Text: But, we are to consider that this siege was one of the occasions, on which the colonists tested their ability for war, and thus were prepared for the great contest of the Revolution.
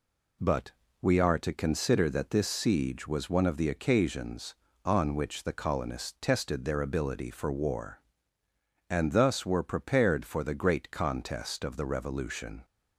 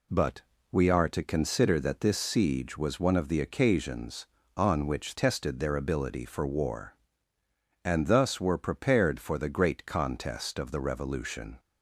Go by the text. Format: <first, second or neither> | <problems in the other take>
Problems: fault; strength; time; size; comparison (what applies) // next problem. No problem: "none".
first | skips "the colonists"; at 5.1 s